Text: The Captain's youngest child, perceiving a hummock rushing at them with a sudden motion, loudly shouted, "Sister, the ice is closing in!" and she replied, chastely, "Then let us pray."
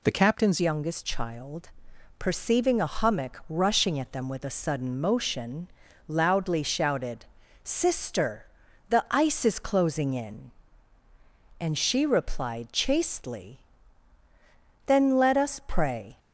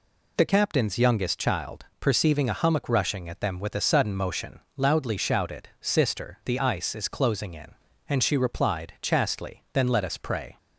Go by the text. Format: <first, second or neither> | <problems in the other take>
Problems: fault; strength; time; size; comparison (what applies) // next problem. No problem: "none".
second | changes voice at "youngest"; from 0.6 s on; 15.5 s long